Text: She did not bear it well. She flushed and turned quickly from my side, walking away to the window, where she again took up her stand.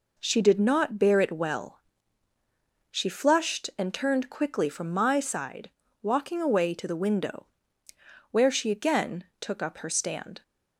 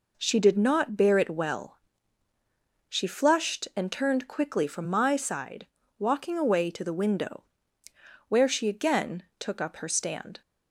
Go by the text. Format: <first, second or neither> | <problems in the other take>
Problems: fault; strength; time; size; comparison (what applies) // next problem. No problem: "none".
neither | pauses between "again" and "took"; slight; the same in both